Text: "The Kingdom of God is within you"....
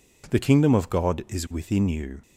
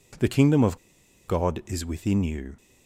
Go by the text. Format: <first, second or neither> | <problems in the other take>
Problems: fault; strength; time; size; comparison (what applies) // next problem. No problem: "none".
first | pauses between "of" and "God"; noticeable; at 0.7 s; 0.49 s long